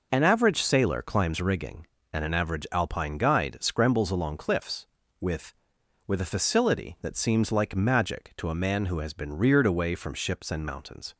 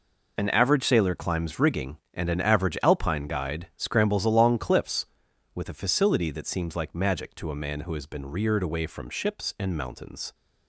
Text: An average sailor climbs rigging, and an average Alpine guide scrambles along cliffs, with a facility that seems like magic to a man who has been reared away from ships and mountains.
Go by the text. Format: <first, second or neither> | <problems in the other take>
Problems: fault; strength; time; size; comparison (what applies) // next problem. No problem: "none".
second | says "with" twice; at 6.0 s